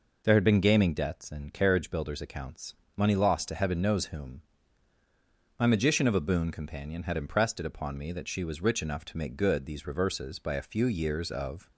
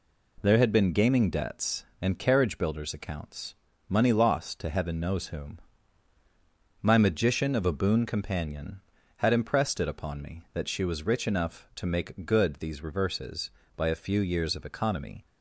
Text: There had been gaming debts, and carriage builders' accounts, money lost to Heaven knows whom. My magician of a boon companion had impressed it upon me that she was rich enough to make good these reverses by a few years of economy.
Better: second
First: stops before "economy"; at 11.7 s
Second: none

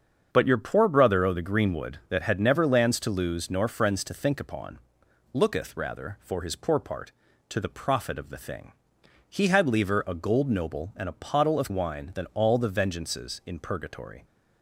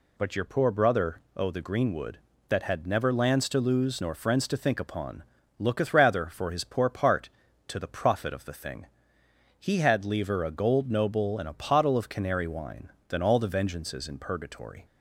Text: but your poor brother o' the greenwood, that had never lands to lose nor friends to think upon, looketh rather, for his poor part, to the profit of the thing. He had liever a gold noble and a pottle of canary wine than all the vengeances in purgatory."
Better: second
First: starts louder than the rest; until 1.3 s; 7 dB // skips "canary"; at 11.6 s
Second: none

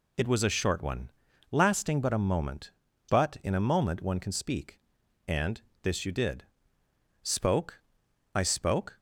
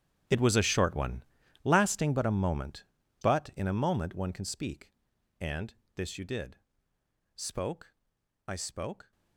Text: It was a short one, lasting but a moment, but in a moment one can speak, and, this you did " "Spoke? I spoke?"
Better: first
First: none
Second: gets quieter; strong; throughout; 25.5 dB

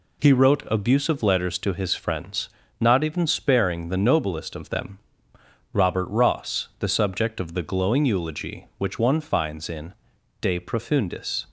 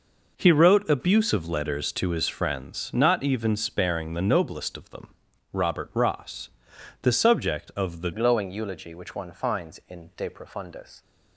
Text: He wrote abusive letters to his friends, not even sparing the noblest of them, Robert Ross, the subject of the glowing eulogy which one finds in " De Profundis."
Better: first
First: none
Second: changes voice at "glowing"; from 8.1 s on; 2.9 s long

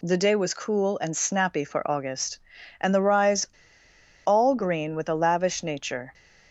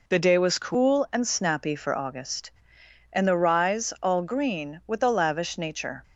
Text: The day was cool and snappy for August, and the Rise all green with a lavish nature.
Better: second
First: pauses between "Rise" and "all"; noticeable; at 3.4 s; 0.78 s long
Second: none

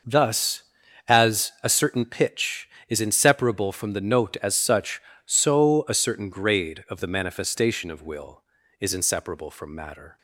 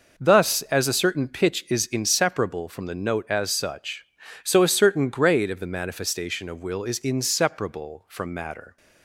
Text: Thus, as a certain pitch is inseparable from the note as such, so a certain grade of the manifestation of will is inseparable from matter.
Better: neither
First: none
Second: none

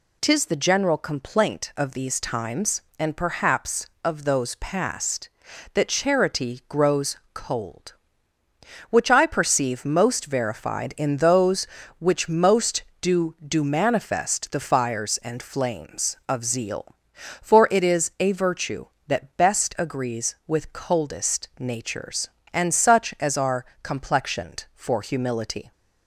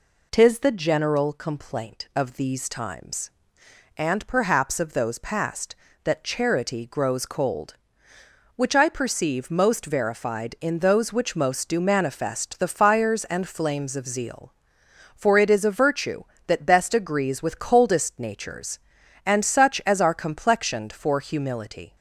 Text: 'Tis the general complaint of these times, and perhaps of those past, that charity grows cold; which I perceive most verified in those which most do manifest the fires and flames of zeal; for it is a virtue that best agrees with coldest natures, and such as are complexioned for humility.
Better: second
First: pauses between "grows" and "cold"; slight; at 7.1 s; 0.16 s long // says "do" twice; at 13.4 s // pauses between "are" and "complexioned"; slight; at 23.6 s; 0.20 s long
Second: none

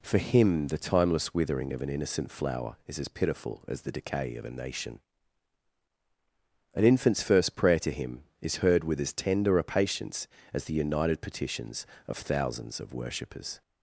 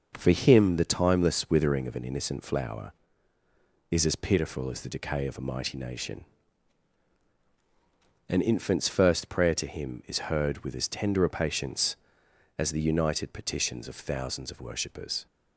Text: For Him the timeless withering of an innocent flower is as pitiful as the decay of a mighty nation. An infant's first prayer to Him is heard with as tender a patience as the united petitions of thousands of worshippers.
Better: second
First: skips "mighty"; at 4.4 s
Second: none

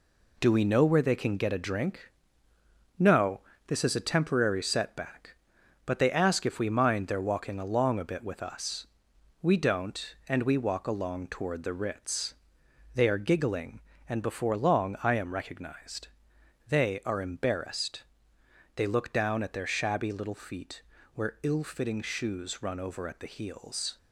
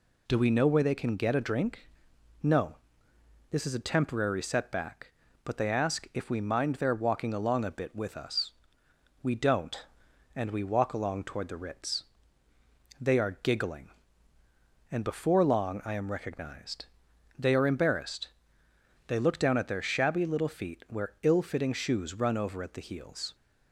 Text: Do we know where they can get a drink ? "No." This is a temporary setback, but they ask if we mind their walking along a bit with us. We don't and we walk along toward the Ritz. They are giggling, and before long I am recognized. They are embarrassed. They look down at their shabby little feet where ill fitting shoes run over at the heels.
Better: second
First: gets quieter; throughout; 6.5 dB // pauses between "feet" and "where"; slight; at 20.8 s; 0.32 s long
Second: none

